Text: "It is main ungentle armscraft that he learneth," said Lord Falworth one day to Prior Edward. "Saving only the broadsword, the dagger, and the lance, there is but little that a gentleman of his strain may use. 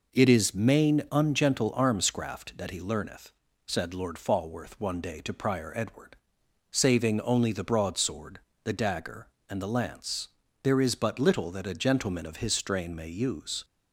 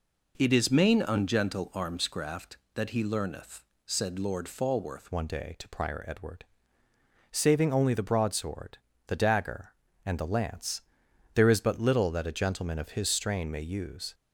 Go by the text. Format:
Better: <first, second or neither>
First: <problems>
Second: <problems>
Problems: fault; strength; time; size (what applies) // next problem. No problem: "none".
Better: first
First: none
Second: changes voice at "one"; from 5.1 s on; 9.0 s long